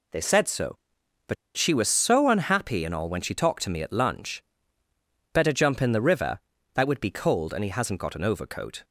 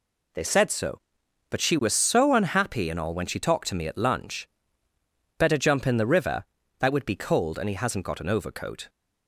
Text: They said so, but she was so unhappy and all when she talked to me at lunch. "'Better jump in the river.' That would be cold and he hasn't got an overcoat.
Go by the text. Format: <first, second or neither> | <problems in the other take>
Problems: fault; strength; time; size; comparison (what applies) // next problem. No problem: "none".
second | pauses between "but" and "she"; slight; at 1.3 s; 0.22 s long